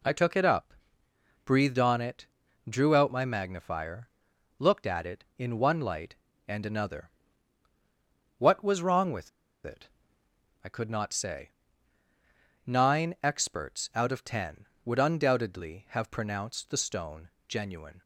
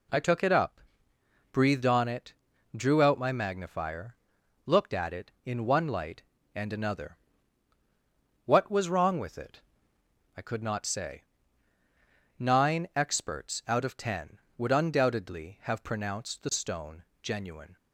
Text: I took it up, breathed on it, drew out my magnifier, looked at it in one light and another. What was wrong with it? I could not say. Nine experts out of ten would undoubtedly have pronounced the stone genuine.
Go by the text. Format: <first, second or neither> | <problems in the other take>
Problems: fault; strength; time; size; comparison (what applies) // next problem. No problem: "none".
second | pauses between "with" and "it"; slight; at 9.2 s; 0.35 s long // pauses between "stone" and "genuine"; slight; at 17.2 s; 0.18 s long; slight in the second